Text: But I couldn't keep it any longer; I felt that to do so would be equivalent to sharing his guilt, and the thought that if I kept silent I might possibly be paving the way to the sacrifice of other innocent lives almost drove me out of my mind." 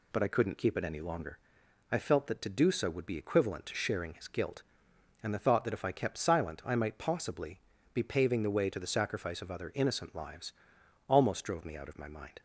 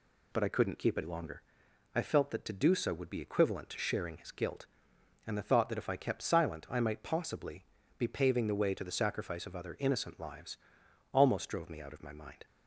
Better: first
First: pauses between "possibly" and "be"; slight; at 7.6 s; 0.32 s long // pauses between "lives" and "almost"; noticeable; at 10.5 s; 0.58 s long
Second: skips "any"; at 1.0 s // pauses between "possibly" and "be"; slight; at 7.6 s; 0.32 s long // pauses between "lives" and "almost"; noticeable; at 10.5 s; 0.58 s long

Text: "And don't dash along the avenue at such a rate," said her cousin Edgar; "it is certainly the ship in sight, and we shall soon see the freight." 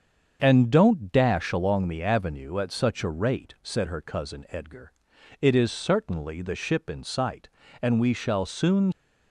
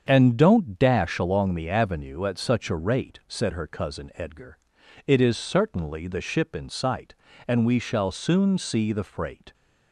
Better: second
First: starts louder than the rest; until 1.4 s; 7 dB // stops before "see the freight"; at 8.9 s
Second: starts louder than the rest; strong; until 1.1 s; 7 dB

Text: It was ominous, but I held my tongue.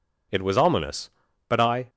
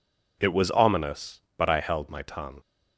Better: second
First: stops before "held my tongue"; at 1.8 s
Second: none

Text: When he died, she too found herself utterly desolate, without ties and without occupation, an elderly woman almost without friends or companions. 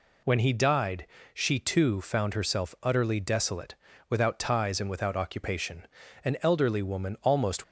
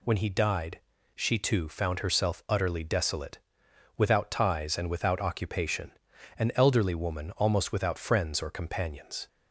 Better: second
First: stops before "without friends or companions"; at 7.6 s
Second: none

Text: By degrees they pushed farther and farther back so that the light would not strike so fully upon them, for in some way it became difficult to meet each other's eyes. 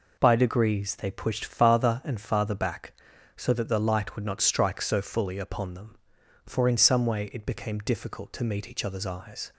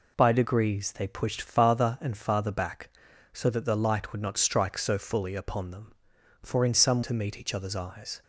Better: first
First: none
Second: skips "way it became difficult"; at 7.0 s

